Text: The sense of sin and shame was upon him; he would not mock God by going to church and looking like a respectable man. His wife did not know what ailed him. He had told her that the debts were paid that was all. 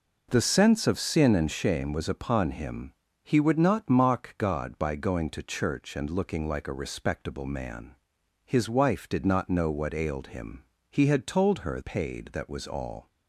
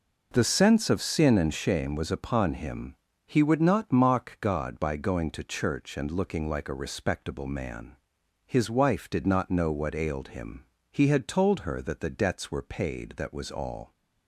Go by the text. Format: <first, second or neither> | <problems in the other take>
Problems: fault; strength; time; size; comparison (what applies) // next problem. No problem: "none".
second | skips "that the debts were"; at 11.8 s